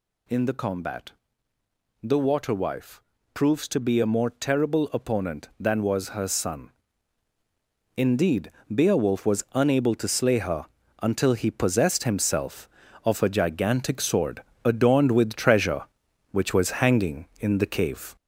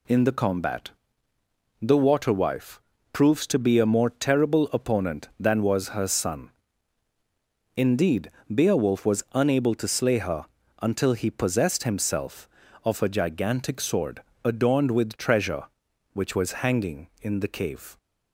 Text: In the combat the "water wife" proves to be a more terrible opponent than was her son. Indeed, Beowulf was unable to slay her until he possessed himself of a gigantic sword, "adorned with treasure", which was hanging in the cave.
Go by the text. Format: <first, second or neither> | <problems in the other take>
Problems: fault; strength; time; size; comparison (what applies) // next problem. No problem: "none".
second | gets louder; noticeable; throughout; 4.5 dB // pauses between "combat" and "the"; noticeable; at 1.1 s; 0.90 s long; noticeable in the second // pauses between "wife" and "proves"; slight; at 3.0 s; 0.32 s long; slight in the second // pauses between "her" and "until"; slight; at 10.6 s; 0.36 s long; slight in the second